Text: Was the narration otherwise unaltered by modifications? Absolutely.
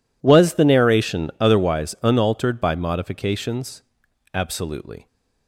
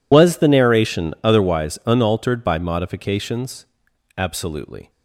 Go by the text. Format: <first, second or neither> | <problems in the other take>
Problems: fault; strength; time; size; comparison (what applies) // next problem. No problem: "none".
first | loses the start of "Was"; at 0.1 s; 60 ms